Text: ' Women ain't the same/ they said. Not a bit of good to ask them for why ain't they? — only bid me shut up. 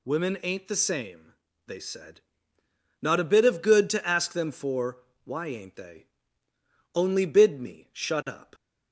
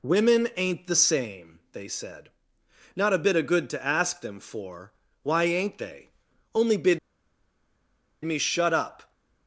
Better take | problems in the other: first | pauses between "for" and "why"; slight; at 4.9 s; 0.30 s long; slight in the first // pauses between "bid" and "me"; at 6.9 s; 1.2 s long

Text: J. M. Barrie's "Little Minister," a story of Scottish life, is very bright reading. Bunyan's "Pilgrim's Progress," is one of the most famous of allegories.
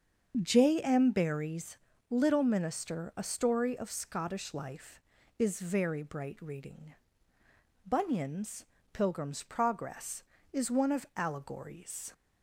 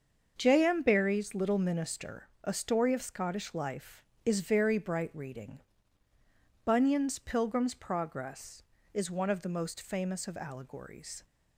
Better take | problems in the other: second | starts louder than the rest; until 1.4 s; 7 dB; also in the second // pauses between "Barrie's" and "Little"; slight; at 1.7 s; 0.32 s long // pauses between "Bunyan's" and "Pilgrim's"; slight; at 8.6 s; 0.26 s long // skips "the most famous of"; at 11.1 s

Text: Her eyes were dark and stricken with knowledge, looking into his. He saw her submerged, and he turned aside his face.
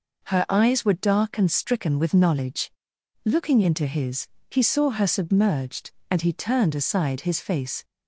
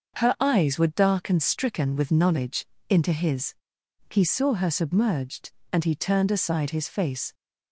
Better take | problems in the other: first | starts louder than the rest; until 1.2 s; 6.5 dB // skips "looking"; at 2.7 s

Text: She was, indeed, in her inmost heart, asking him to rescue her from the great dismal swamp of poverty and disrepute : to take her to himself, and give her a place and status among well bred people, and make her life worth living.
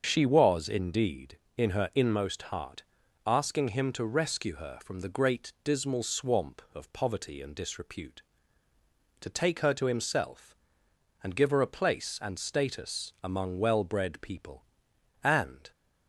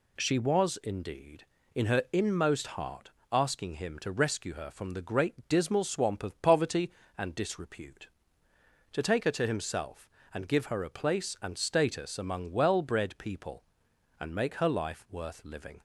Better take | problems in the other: second | starts louder than the rest; until 1.0 s; 6.5 dB // stops before "make her life worth living"; at 15.7 s

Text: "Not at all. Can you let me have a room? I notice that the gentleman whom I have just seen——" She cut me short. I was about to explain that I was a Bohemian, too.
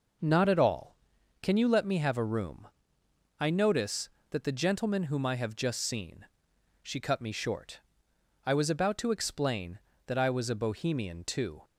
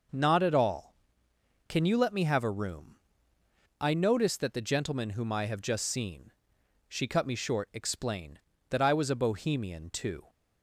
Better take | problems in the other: first | skips "I was about to"; at 7.7 s

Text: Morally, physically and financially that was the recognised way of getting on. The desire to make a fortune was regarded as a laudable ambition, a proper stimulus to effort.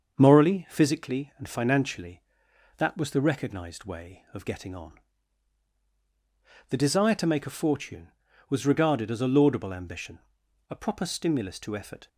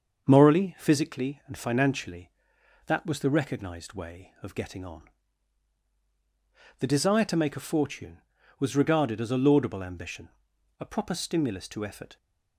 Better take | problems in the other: neither | starts louder than the rest; the same in both

